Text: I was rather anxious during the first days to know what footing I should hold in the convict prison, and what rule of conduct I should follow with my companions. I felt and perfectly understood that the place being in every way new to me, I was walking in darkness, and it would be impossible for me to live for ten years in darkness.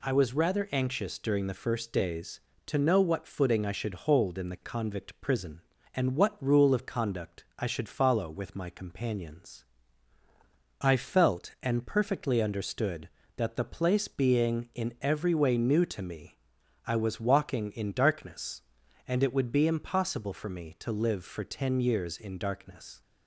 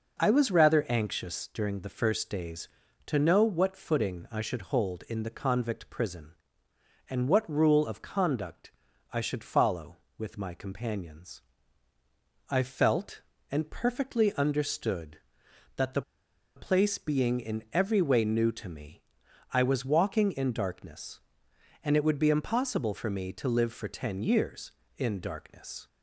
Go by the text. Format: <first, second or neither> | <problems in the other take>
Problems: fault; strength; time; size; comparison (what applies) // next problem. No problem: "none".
first | pauses between "conduct" and "I"; at 8.7 s; 0.42 s long // pauses between "the" and "place"; noticeable; at 16.0 s; 0.55 s long